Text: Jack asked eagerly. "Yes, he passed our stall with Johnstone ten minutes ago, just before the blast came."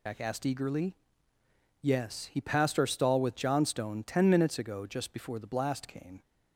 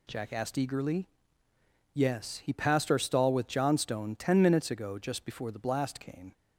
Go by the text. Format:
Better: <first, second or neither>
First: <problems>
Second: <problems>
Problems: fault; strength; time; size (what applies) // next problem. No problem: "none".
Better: second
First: loses the start of "Jack"; at 0.0 s; 100 ms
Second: none